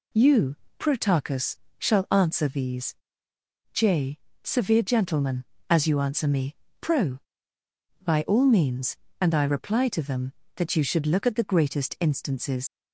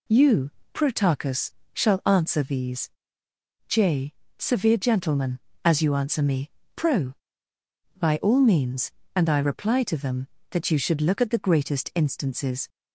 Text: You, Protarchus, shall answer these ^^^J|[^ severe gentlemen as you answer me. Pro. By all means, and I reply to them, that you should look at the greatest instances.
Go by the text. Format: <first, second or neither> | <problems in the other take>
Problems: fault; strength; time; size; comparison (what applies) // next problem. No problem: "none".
second | pauses between "these" and "J"; noticeable; at 2.9 s; 0.78 s long; noticeable in the second // leaves "instances" unfinished; at 12.6 s; 65 ms